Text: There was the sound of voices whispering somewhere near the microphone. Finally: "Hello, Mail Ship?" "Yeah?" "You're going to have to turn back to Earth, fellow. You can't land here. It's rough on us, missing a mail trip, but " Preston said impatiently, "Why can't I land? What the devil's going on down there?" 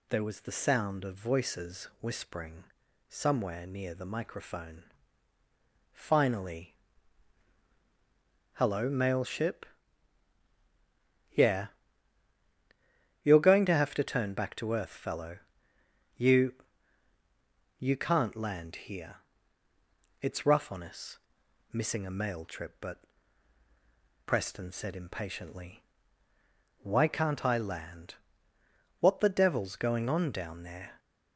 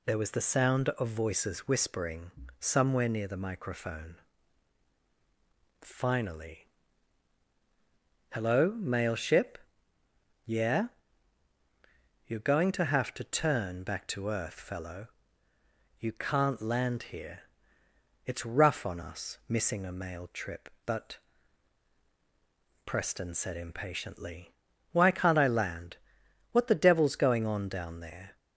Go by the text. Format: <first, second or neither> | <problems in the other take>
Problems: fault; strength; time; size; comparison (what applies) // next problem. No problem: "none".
second | pauses between "whispering" and "somewhere"; at 2.6 s; 0.44 s long; slight in the second // says "You" twice; at 17.7 s